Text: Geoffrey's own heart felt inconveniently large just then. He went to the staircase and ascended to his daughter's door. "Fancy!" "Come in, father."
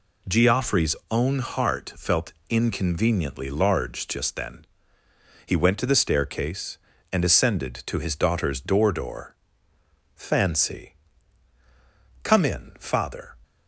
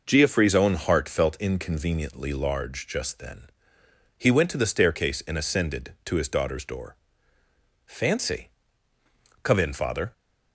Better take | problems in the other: second | pauses between "Geoffrey's" and "own"; slight; at 0.9 s; 0.16 s long // pauses between "felt" and "inconveniently"; slight; at 2.3 s; 0.16 s long // says "door" twice; at 8.9 s

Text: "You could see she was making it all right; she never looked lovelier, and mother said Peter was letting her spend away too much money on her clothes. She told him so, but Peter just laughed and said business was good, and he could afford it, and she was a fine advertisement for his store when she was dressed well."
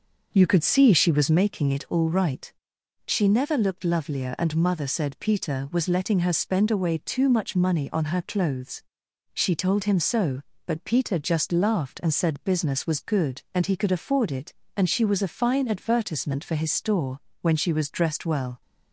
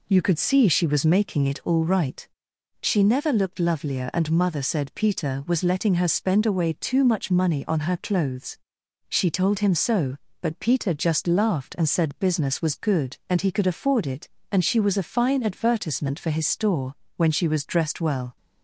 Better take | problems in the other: second | starts louder than the rest; noticeable; until 1.4 s; 5.5 dB // pauses between "store" and "when"; slight; at 17.1 s; 0.22 s long; slight in the second

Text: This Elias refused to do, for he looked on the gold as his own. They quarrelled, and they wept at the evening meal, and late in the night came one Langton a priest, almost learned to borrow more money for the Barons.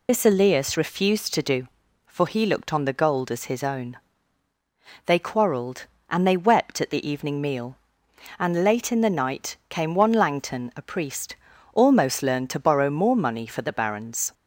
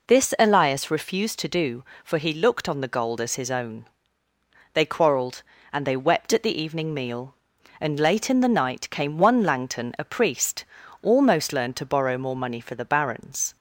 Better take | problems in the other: second | loses the start of "This"; at 0.0 s; 40 ms

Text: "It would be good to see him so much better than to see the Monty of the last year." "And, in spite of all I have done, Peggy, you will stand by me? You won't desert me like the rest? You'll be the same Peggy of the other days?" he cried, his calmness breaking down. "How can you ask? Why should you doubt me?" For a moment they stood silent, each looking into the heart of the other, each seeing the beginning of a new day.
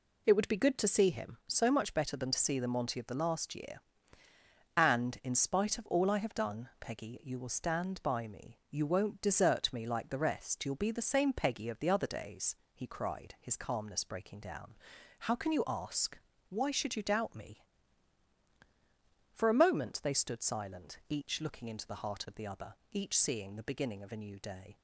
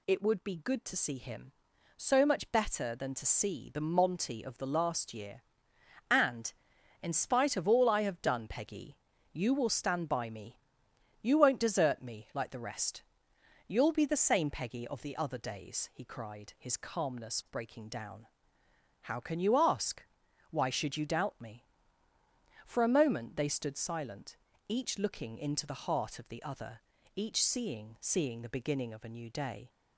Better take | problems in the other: first | says "seeing" twice; at 27.9 s

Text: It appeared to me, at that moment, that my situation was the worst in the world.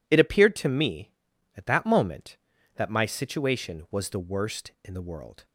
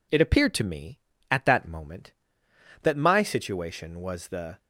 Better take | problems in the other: first | stops before "worst in the world"; at 4.5 s

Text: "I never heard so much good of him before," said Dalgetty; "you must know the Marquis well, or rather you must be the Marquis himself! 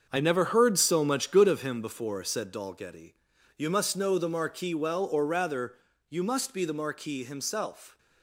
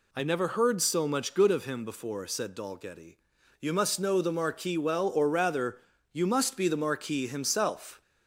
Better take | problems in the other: second | gets quieter; strong; throughout; 9 dB // pauses between "rather" and "you"; slight; at 5.7 s; 0.32 s long; slight in the second

